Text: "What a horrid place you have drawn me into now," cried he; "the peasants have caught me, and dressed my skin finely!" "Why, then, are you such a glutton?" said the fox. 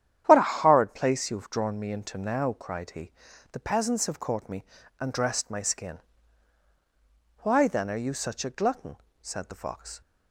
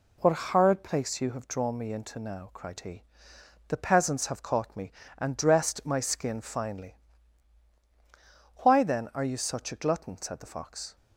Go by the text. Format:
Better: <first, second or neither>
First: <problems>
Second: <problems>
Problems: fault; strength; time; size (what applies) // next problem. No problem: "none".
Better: second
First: starts louder than the rest; strong; until 1.2 s; 10 dB // skips "finely"; at 6.6 s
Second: none